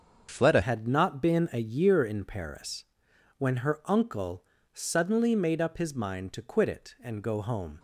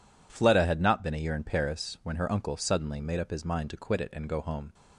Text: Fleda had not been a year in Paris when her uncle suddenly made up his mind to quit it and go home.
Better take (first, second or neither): second